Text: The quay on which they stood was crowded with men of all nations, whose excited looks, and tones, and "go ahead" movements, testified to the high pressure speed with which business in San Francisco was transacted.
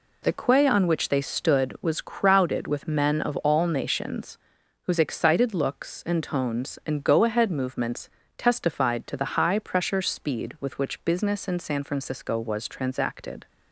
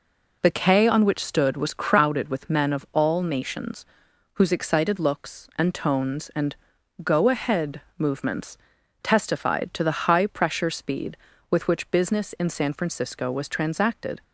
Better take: first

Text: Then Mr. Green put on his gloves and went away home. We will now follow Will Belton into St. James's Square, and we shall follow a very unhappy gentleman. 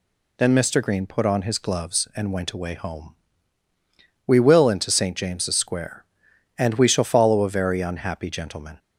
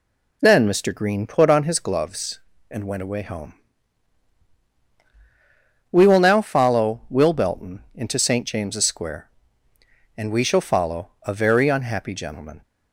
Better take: second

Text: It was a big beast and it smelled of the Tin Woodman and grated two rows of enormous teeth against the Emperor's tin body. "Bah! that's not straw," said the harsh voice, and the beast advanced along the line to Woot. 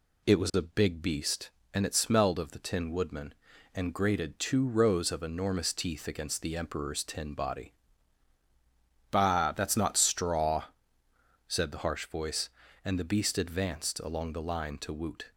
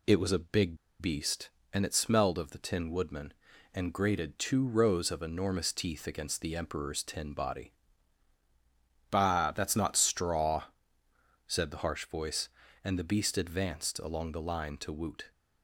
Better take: first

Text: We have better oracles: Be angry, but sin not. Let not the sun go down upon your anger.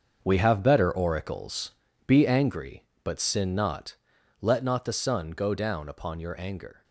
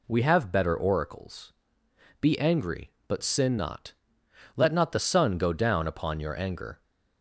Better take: second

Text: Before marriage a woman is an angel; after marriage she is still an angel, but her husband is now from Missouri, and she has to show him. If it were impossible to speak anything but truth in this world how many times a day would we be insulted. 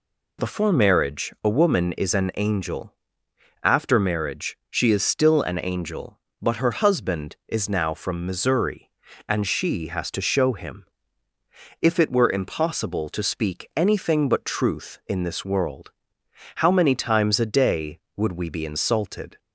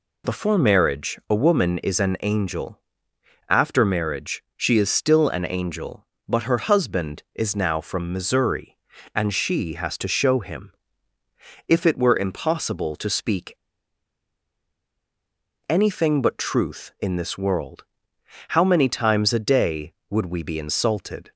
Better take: first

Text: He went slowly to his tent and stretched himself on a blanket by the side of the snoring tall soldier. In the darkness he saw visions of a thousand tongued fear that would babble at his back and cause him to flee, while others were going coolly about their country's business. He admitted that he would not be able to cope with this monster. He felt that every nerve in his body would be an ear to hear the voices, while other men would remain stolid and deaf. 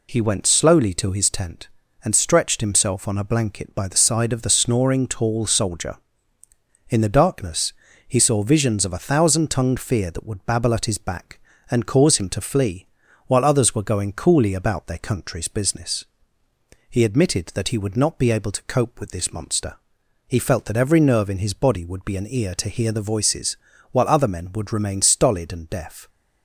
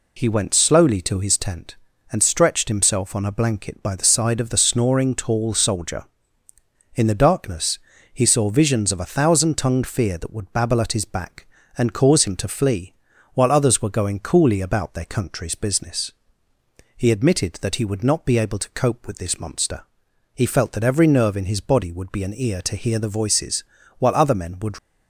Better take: first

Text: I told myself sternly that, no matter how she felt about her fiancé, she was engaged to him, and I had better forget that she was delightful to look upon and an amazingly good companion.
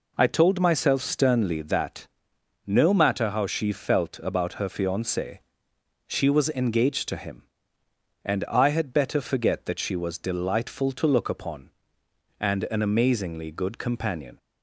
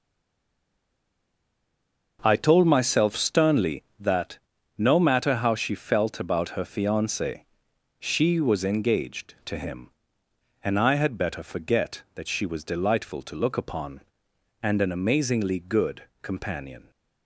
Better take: first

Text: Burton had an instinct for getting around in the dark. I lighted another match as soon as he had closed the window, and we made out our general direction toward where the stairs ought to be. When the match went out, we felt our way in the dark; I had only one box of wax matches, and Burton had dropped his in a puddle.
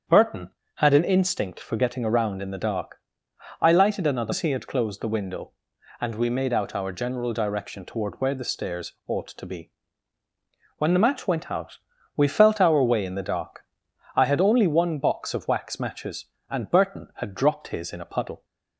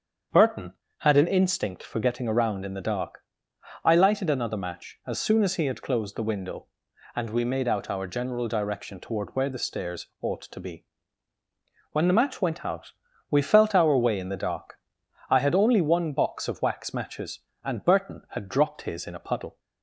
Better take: second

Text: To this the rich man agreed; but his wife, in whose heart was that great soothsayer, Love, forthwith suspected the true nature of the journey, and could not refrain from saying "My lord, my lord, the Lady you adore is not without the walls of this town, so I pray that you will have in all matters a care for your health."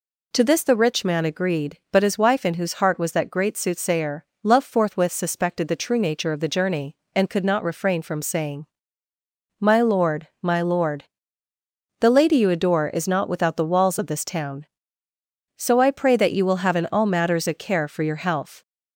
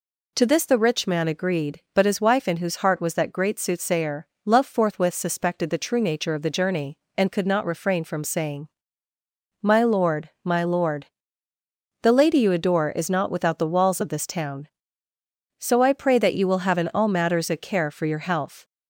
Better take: neither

